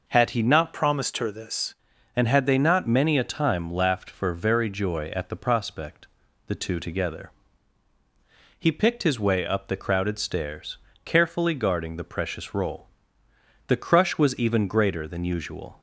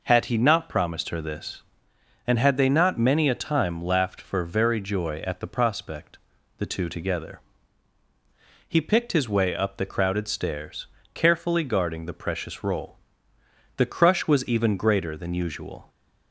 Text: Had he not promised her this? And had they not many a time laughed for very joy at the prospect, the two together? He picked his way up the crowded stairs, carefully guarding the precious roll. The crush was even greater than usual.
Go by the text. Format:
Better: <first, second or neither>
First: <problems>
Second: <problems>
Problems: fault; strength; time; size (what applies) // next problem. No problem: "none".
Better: second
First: changes voice from "promised" to "this"; from 0.7 to 1.7 s; 1.0 s long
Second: none